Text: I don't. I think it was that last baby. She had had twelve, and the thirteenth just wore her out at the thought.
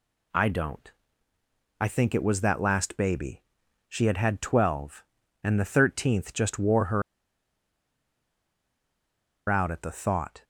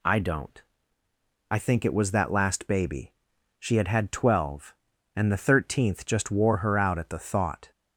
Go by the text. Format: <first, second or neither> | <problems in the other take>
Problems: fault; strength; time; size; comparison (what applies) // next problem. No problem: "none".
second | pauses between "her" and "out"; strong; at 7.0 s; 2.4 s long